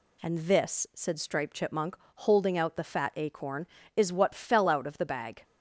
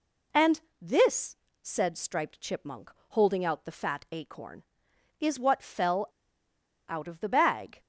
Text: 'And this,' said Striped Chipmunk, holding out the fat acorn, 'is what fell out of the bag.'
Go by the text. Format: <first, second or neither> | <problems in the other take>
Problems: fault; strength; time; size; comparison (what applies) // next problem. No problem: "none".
first | pauses between "And" and "this"; slight; at 0.6 s; 0.20 s long // pauses between "fell" and "out"; noticeable; at 6.0 s; 0.82 s long